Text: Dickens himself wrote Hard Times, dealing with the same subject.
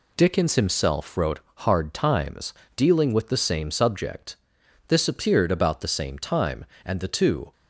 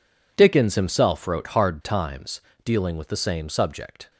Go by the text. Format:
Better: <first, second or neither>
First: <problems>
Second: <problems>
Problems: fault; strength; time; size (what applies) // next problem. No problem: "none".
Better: second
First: pauses between "wrote" and "Hard"; slight; at 1.3 s; 0.16 s long // goes on to say "This appeared about the same time and the two"; strong; from 4.8 s on; 2.6 s long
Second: none